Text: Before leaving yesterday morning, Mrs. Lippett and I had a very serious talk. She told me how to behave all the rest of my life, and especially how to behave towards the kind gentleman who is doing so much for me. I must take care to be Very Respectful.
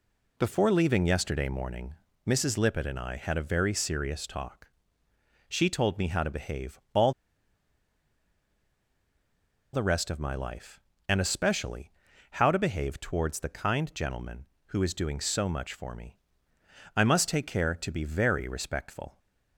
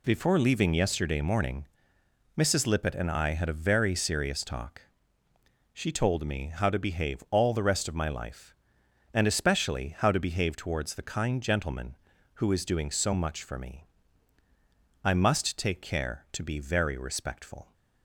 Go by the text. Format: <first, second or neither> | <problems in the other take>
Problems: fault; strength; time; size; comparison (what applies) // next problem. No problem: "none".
second | pauses between "all" and "the"; strong; at 7.1 s; 2.6 s long // pauses between "especially" and "how"; at 11.9 s; 0.40 s long